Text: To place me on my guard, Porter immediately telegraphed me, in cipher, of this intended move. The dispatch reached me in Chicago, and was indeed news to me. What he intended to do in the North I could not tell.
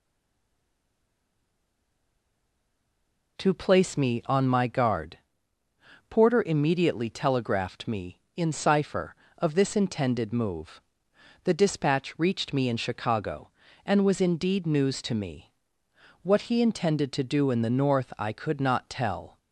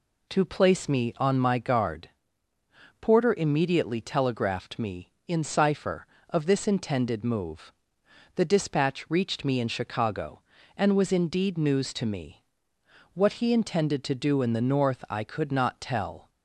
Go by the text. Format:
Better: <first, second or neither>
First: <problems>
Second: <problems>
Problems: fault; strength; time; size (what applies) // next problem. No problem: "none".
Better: second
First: stays silent before the first word; strong; until 3.3 s; 3.3 s long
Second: none